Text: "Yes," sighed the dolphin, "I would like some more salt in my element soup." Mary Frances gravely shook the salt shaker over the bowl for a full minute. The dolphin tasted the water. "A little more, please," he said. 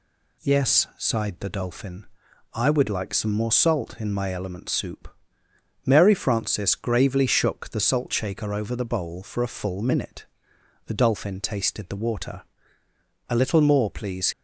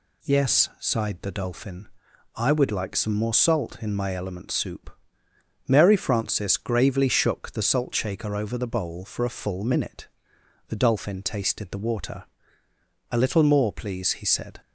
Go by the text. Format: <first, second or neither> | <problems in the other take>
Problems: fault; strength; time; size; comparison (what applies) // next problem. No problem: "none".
second | stops before "he said"; at 14.3 s